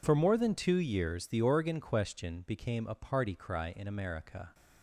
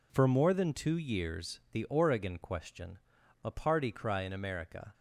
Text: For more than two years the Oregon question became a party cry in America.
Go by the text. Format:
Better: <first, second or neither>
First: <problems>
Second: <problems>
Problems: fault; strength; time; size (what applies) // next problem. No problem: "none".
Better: first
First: none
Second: skips "became"; at 3.2 s